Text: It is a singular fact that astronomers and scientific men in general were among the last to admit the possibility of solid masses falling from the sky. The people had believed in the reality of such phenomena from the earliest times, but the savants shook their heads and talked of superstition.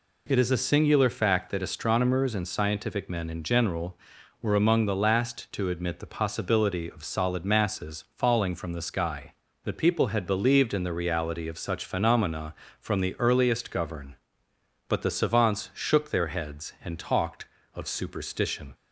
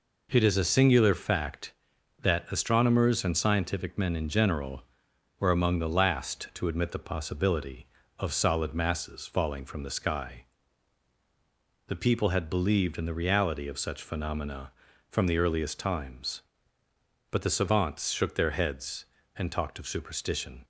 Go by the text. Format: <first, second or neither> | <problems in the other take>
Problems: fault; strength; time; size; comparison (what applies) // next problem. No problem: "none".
second | says "govern" for "times"; at 13.7 s